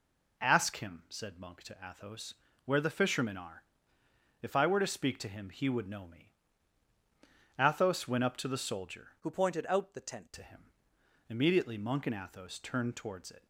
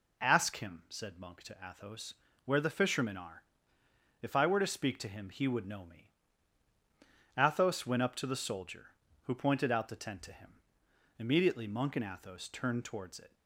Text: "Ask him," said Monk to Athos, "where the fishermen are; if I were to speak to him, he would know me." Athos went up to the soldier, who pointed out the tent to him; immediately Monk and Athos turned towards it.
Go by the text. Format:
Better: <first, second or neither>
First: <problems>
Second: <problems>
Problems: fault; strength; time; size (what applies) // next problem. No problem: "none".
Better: second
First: changes voice from "who" to "tent"; from 9.1 to 10.3 s; 1.2 s long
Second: none